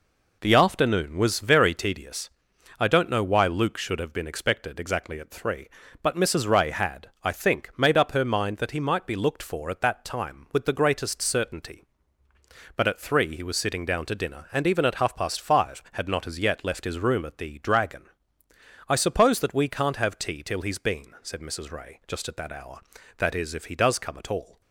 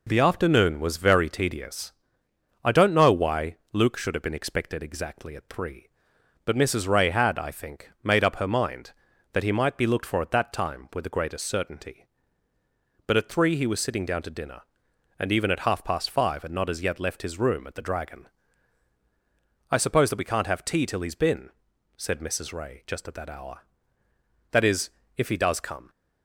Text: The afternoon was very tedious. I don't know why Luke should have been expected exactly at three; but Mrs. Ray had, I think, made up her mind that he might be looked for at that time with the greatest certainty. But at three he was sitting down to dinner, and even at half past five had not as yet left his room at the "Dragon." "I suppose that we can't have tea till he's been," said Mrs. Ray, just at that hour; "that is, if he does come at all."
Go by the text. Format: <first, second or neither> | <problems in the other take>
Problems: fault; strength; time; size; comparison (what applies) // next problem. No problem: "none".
first | pauses between "why" and "Luke"; slight; at 3.5 s; 0.18 s long // stops before "at all"; at 25.8 s